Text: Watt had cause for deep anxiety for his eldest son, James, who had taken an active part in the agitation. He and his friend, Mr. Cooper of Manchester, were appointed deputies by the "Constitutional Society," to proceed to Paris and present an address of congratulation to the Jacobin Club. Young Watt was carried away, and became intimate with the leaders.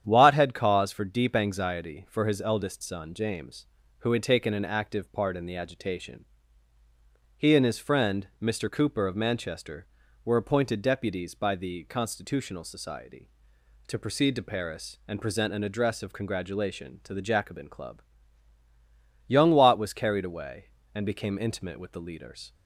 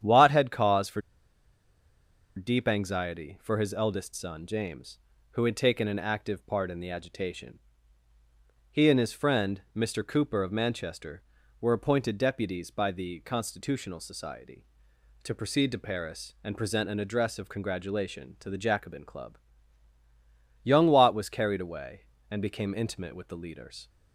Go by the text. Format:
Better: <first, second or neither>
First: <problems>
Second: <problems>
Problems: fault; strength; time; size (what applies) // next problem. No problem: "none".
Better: first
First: starts louder than the rest; strong; until 1.0 s; 9.5 dB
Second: starts louder than the rest; strong; until 2.3 s; 9.5 dB // pauses between "for" and "deep"; strong; at 0.9 s; 1.3 s long